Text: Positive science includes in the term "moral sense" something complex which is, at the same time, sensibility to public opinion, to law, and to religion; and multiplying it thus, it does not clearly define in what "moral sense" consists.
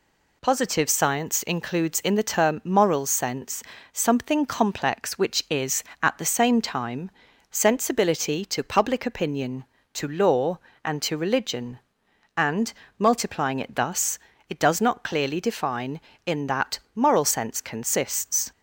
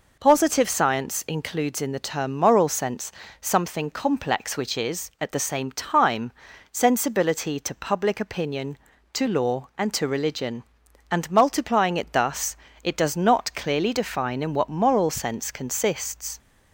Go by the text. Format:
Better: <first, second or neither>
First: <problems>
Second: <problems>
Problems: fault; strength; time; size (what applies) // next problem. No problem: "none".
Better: second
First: pauses between "sense" and "something"; slight; at 3.6 s; 0.30 s long // pauses between "and" and "multiplying"; slight; at 12.7 s; 0.26 s long // says "that" for "what"; at 16.4 s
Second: pauses between "sense" and "something"; slight; at 3.1 s; 0.30 s long